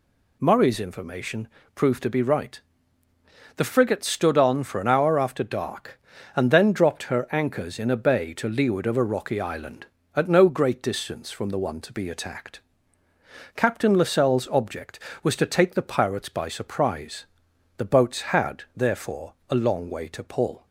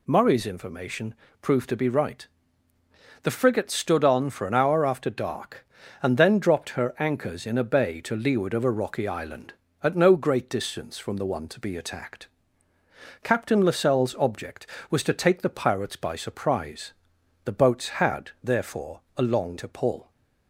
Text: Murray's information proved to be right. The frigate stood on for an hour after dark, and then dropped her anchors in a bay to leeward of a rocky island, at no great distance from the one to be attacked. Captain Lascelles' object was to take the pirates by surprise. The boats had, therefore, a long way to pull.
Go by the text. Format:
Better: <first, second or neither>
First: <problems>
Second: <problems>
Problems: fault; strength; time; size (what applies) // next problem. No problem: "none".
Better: first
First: pauses between "information" and "proved"; slight; at 1.4 s; 0.26 s long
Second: pauses between "information" and "proved"; slight; at 1.1 s; 0.26 s long // skips "way"; at 19.5 s